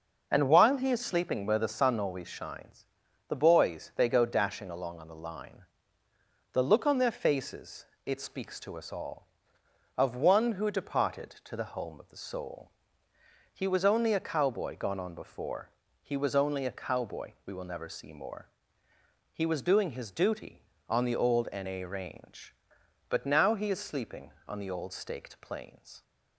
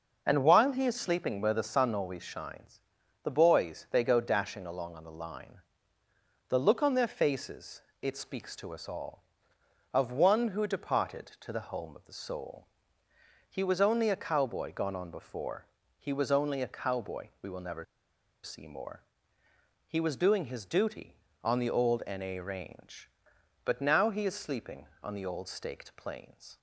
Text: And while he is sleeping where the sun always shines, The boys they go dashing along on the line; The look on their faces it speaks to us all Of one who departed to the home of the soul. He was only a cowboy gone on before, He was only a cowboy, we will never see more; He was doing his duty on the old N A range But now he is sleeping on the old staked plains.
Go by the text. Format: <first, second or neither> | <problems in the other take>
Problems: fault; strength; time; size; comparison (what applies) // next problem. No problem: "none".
first | pauses between "faces" and "it"; slight; at 7.8 s; 0.20 s long; slight in the first // pauses between "never" and "see"; noticeable; at 17.8 s; 0.59 s long